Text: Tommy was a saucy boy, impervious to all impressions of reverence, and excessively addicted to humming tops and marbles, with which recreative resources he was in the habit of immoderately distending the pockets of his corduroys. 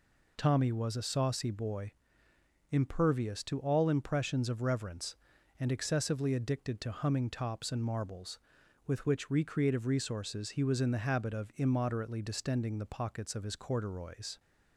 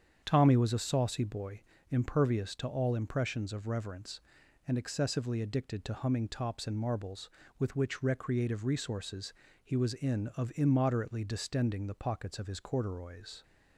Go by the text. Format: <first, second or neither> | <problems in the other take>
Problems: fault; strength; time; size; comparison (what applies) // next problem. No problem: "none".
first | starts louder than the rest; strong; until 1.2 s; 8 dB // pauses between "resources" and "he"; slight; at 9.3 s; 0.30 s long // skips "the habit"; at 10.3 s